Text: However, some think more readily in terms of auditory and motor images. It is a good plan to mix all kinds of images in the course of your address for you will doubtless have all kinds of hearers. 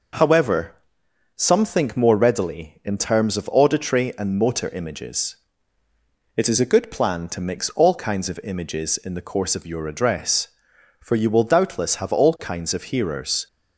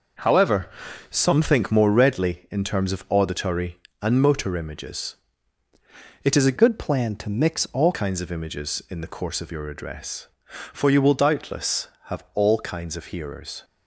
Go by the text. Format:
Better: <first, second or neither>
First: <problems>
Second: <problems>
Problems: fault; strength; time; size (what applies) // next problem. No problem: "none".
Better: first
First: none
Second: changes voice from "good" to "all"; from 6.5 to 7.9 s; 1.4 s long